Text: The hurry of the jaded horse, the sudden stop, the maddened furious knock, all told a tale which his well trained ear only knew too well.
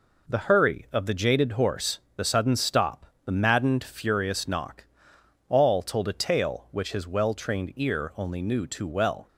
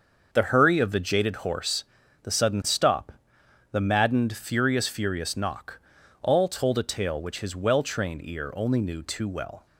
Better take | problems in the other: first | starts louder than the rest; until 1.3 s; 6.5 dB // says "furious" twice; at 4.8 s

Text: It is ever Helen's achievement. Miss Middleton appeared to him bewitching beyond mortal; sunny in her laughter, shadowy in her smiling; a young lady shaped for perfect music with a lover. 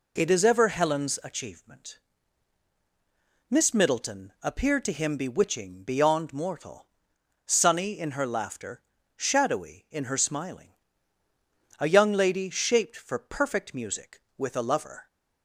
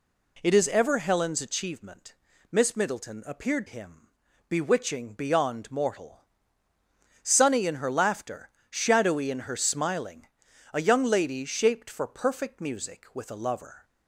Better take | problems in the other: first | skips "to"; at 3.6 s // pauses between "him" and "bewitching"; at 4.0 s; 0.42 s long

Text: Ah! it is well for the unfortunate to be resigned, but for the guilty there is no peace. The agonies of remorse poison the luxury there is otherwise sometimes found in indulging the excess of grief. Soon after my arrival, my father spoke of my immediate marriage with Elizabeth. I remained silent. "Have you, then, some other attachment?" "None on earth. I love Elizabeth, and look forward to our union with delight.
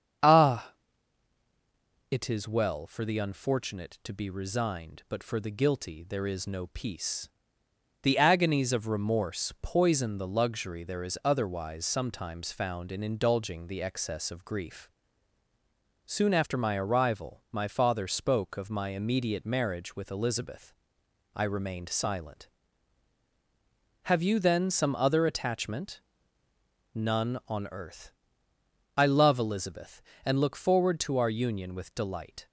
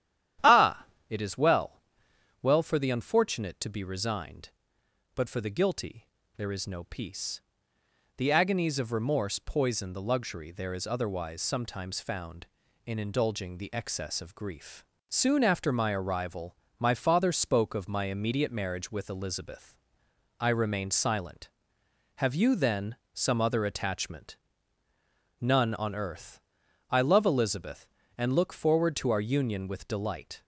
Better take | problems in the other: first | starts louder than the rest; strong; until 1.6 s; 11 dB; strong in the first // says "well" twice; at 2.4 s // pauses between "guilty" and "there"; slight; at 6.0 s; 0.32 s long

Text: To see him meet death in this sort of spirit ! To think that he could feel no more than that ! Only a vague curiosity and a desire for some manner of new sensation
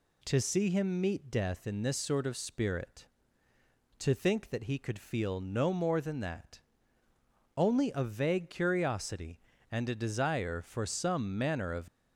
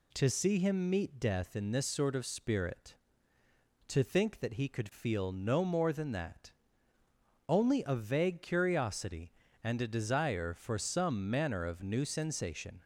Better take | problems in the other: second | stops before "new sensation"; at 11.8 s

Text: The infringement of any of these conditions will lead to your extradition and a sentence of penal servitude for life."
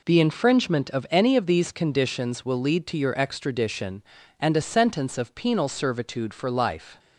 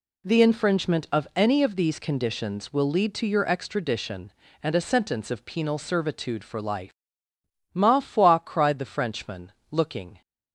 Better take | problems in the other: first | goes on to say "Ma foi cried the Frenchman looking"; strong; from 7.7 s on; 2.4 s long

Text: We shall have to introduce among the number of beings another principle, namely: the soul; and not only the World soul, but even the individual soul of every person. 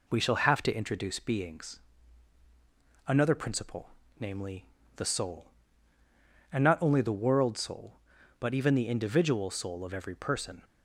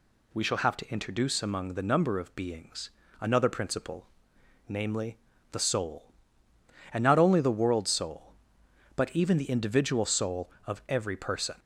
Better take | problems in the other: second | skips "among the number of"; at 1.1 s // pauses between "beings" and "another"; strong; at 1.7 s; 1.3 s long; slight in the second

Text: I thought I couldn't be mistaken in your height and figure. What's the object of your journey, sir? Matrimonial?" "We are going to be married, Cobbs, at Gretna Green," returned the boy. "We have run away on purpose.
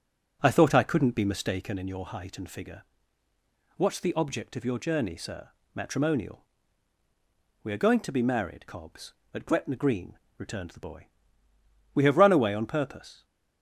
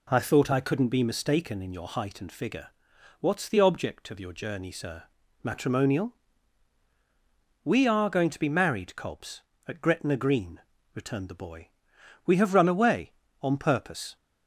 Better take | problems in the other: second | starts louder than the rest; strong; until 1.8 s; 7 dB

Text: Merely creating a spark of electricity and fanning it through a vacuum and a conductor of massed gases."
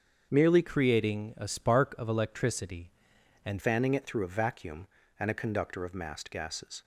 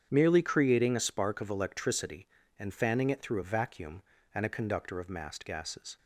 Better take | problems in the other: second | starts louder than the rest; until 1.3 s; 7 dB; strong in the second // changes voice from "creating" to "and"; from 0.6 to 3.5 s; 2.9 s long

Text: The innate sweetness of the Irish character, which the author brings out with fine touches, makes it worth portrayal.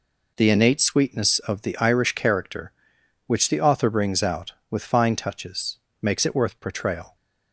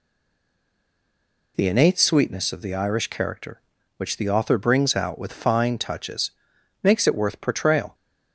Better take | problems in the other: first | stays silent before the first word; noticeable; until 1.5 s; 1.5 s long

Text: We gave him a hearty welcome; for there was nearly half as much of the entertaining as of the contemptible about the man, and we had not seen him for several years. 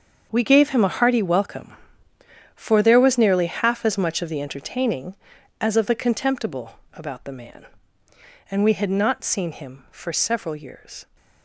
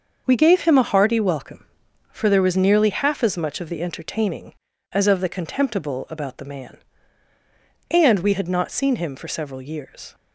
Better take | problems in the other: second | gets quieter; strong; throughout; 13 dB // starts louder than the rest; until 1.3 s; 6.5 dB; also in the second // pauses between "contemptible" and "about"; slight; at 6.7 s; 0.16 s long

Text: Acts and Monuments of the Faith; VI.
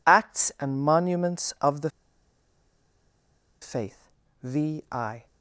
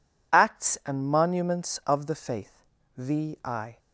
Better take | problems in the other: second | pauses between "the" and "Faith"; strong; at 1.9 s; 1.7 s long

